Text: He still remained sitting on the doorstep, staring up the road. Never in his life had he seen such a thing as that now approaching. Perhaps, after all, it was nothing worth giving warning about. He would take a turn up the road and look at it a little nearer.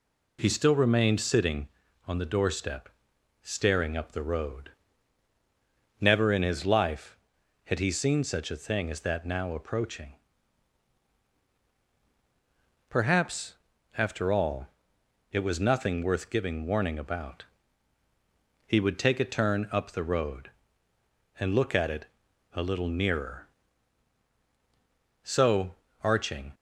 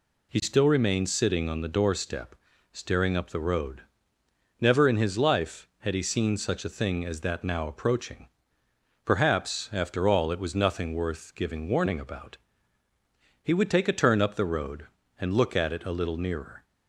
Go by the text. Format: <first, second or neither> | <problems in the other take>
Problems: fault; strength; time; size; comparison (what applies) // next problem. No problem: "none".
second | pauses between "it" and "a"; noticeable; at 22.0 s; 0.46 s long // goes on to say "So arching"; from 25.2 s on; 1.3 s long